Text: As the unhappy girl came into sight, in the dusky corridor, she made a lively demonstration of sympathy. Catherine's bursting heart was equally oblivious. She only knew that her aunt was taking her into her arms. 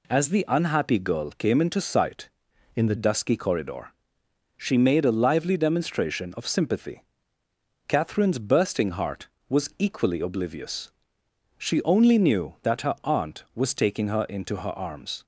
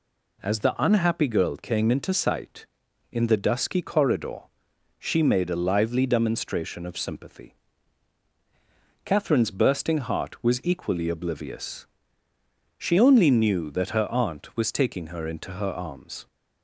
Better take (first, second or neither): second